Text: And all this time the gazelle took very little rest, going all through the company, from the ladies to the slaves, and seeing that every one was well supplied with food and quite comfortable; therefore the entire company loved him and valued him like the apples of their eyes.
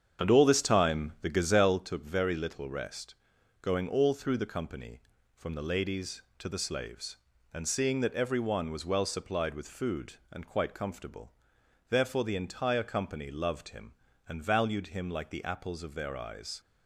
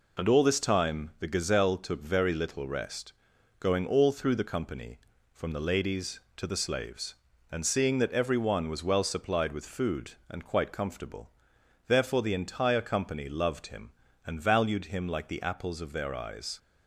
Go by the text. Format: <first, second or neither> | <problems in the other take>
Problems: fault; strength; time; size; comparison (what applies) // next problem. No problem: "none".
second | starts louder than the rest; strong; until 2.0 s; 8 dB